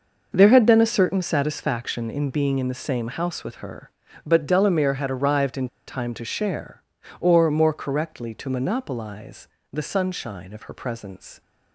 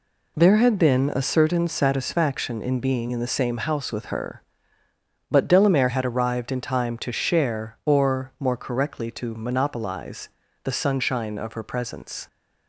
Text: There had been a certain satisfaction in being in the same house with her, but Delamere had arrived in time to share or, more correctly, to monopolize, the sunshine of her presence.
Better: second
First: pauses between "in" and "time"; slight; at 5.6 s; 0.20 s long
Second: none

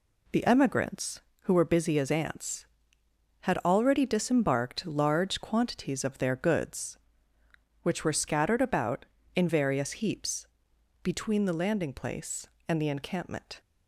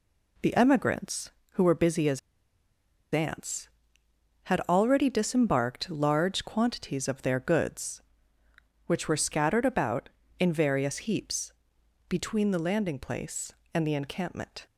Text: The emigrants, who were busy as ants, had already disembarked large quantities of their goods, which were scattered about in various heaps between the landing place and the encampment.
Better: first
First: pauses between "heaps" and "between"; noticeable; at 10.4 s; 0.56 s long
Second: pauses between "as" and "ants"; noticeable; at 2.1 s; 0.94 s long // pauses between "heaps" and "between"; noticeable; at 11.5 s; 0.56 s long

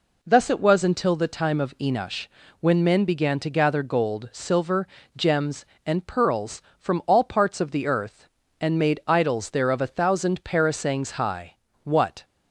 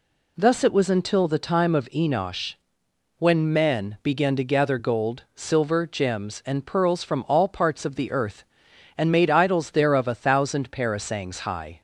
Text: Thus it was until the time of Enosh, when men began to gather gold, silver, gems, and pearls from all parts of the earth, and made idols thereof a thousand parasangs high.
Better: second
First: goes on to say "What"; slight; from 11.8 s on; 0.40 s long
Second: none

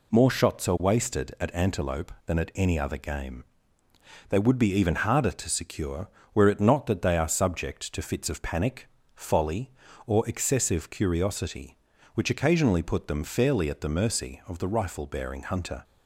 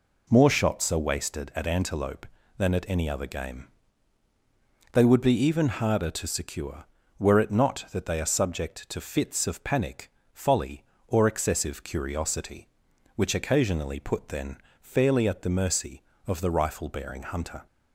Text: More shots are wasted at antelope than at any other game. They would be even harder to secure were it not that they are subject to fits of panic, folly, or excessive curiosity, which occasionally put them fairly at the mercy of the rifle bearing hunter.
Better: first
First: none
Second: says "then" for "them"; at 14.2 s

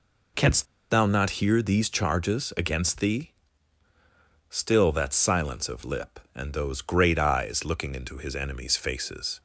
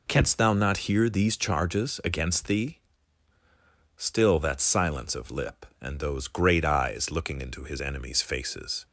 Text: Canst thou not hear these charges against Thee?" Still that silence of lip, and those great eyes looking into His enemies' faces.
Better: second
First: pauses between "Canst" and "thou"; slight; at 0.6 s; 0.25 s long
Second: none

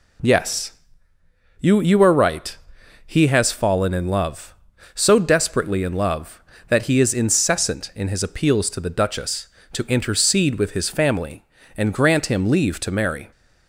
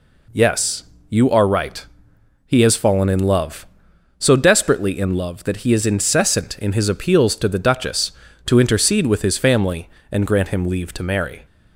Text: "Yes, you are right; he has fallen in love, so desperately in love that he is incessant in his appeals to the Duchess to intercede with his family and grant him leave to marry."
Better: second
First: says "you" twice; at 1.8 s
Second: none

